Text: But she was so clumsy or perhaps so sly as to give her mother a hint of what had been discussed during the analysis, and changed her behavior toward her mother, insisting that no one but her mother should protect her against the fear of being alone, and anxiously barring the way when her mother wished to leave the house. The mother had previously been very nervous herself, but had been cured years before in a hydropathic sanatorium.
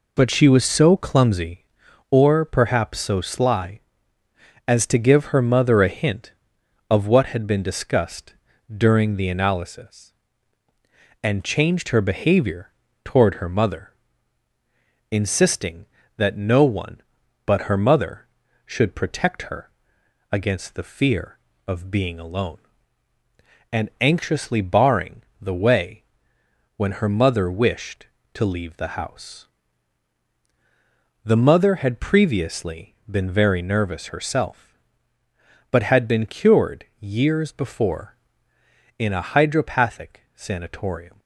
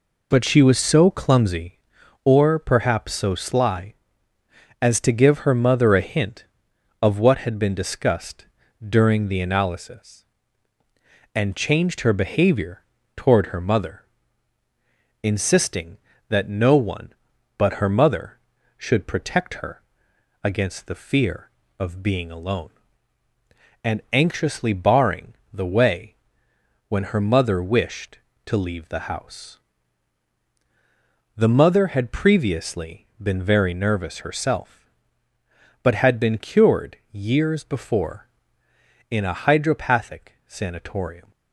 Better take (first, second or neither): neither